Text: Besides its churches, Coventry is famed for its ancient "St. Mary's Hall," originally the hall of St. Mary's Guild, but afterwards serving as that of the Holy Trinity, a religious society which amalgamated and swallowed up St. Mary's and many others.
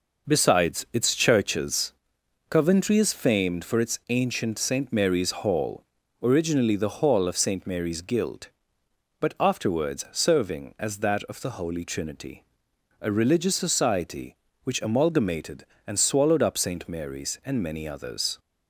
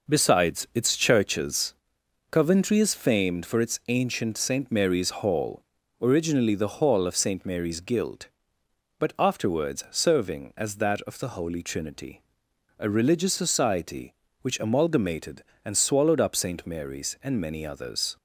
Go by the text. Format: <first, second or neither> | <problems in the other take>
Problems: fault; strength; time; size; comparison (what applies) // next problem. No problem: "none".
neither | none